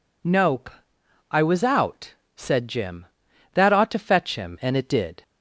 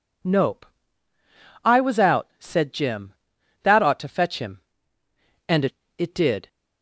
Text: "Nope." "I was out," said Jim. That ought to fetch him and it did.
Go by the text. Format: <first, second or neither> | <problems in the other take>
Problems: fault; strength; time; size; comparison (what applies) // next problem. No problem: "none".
first | says "it" twice; at 5.9 s